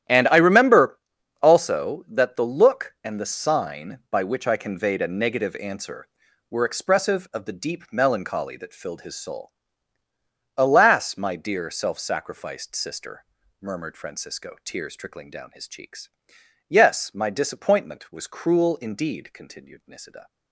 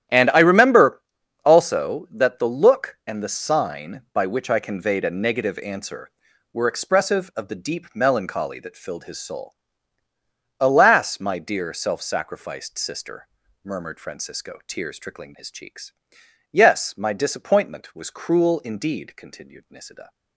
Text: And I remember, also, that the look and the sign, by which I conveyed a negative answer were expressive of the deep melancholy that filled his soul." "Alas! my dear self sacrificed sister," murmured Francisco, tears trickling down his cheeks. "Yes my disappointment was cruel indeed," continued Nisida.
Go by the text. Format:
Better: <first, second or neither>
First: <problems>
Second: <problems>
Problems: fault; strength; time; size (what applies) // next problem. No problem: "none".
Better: first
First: starts louder than the rest; strong; until 1.5 s; 11.5 dB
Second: starts louder than the rest; strong; until 1.5 s; 11 dB // skips "down"; at 15.3 s